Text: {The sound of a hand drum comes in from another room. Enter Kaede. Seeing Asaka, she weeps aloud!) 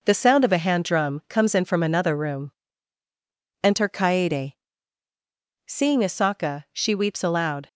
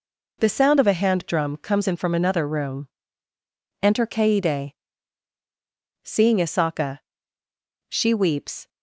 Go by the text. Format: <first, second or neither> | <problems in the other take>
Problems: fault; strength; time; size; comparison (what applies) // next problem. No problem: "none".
first | stops before "aloud"; at 8.6 s